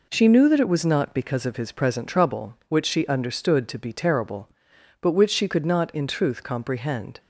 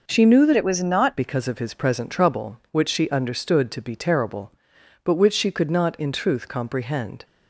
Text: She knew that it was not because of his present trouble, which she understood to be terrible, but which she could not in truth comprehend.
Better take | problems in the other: first | changes voice from "it" to "not"; from 0.5 to 1.1 s; 0.6 s long

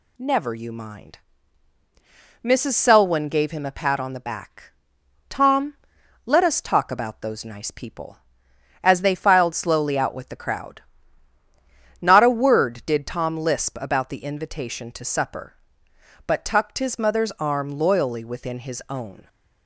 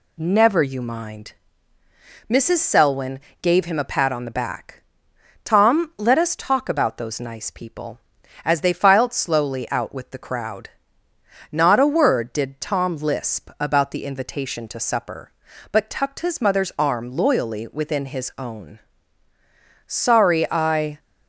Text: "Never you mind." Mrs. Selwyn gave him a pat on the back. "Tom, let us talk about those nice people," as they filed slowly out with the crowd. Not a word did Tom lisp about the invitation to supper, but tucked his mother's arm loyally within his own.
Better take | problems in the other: first | pauses between "Selwyn" and "gave"; slight; at 3.2 s; 0.20 s long // goes on to say "Sorry I"; noticeable; from 19.8 s on; 1.1 s long

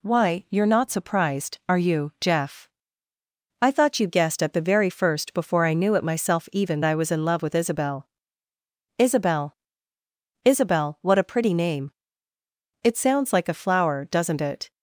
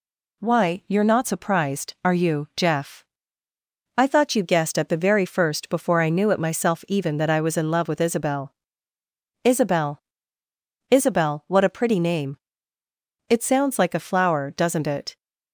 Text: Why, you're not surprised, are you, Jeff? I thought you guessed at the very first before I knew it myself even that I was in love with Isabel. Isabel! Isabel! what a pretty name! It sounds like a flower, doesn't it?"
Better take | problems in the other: second | skips "that"; at 6.8 s

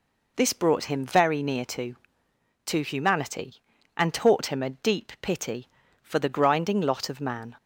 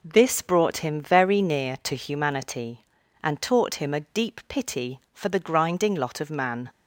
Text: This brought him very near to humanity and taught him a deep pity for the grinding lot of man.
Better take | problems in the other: second | says "to" twice; at 2.6 s

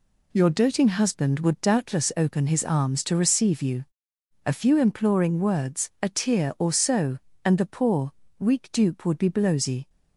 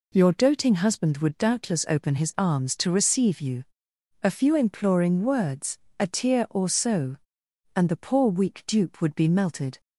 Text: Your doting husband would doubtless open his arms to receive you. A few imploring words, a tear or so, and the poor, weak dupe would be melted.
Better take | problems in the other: second | says "blowsy" for "melted"; at 9.2 s

